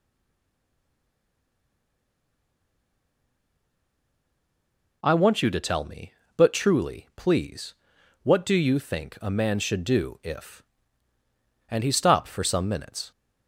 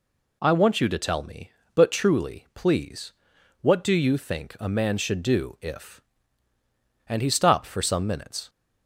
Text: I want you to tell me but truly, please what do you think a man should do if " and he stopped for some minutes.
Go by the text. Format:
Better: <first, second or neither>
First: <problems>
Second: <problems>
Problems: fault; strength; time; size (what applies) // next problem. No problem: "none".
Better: second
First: stays silent before the first word; strong; until 5.0 s; 5.0 s long // pauses between "please" and "what"; noticeable; at 7.7 s; 0.48 s long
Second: pauses between "please" and "what"; noticeable; at 3.1 s; 0.48 s long